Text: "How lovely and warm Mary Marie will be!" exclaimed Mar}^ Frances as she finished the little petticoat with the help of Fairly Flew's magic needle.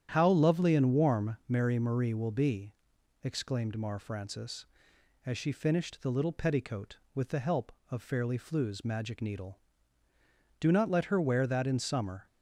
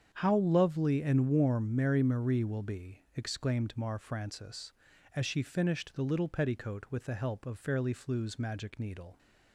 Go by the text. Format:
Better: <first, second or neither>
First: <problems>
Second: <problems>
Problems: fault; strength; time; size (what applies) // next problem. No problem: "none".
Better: second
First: starts louder than the rest; strong; until 1.1 s; 10 dB // goes on to say "Do not let her wear that in summer"; strong; from 10.5 s on; 1.6 s long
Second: starts louder than the rest; strong; until 1.1 s; 7.5 dB